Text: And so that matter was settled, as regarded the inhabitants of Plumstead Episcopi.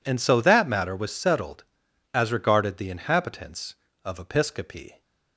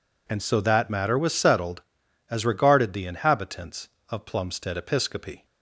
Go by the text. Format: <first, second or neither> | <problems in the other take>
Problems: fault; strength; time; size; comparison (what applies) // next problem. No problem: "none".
second | skips "Plumstead"; at 4.1 s